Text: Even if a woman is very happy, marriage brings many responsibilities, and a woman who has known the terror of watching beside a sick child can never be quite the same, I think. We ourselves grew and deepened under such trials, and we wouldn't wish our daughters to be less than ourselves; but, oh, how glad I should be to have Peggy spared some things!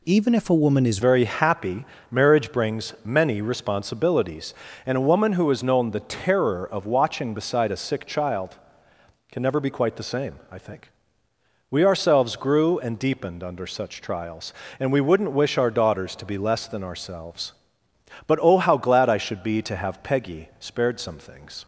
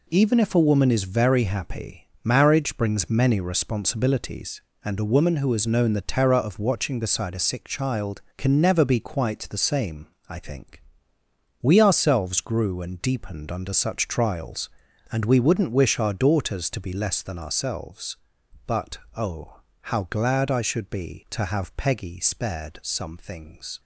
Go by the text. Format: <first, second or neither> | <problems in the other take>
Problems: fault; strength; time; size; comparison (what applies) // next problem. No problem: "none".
second | changes voice at "very"; from 1.0 s on; 20.6 s long